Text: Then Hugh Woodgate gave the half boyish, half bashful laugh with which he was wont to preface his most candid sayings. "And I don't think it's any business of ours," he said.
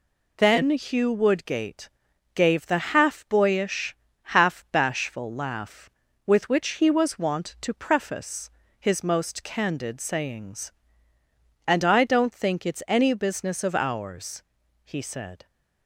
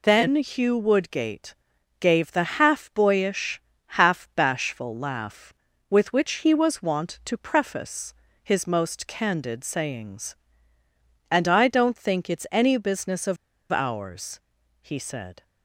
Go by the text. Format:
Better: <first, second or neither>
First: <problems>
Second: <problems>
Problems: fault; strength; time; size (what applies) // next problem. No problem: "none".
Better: first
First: pauses between "Woodgate" and "gave"; noticeable; at 1.8 s; 0.46 s long // pauses between "preface" and "his"; slight; at 8.4 s; 0.30 s long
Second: pauses between "Woodgate" and "gave"; noticeable; at 1.5 s; 0.46 s long // pauses between "preface" and "his"; slight; at 8.1 s; 0.30 s long // pauses between "of" and "ours"; at 13.3 s; 0.36 s long